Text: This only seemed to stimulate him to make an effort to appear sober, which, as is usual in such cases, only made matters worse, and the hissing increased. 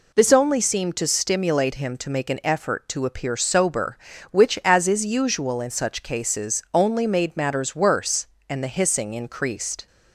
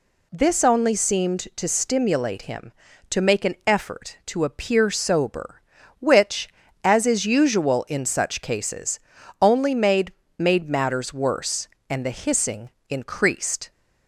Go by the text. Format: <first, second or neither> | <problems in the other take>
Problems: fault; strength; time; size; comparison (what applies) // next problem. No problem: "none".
first | says "made" twice; at 10.3 s // pauses between "hissing" and "increased"; slight; at 12.6 s; 0.20 s long